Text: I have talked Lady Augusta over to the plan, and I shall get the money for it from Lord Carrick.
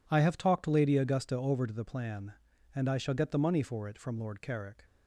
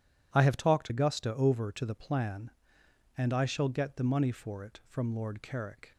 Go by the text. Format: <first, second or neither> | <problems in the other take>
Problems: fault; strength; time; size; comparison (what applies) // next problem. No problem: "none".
first | skips "Lady"; at 0.8 s